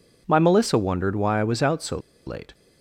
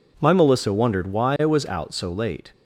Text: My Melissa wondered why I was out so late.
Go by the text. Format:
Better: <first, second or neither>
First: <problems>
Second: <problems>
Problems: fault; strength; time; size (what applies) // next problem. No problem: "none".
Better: second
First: pauses between "so" and "late"; slight; at 1.9 s; 0.28 s long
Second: none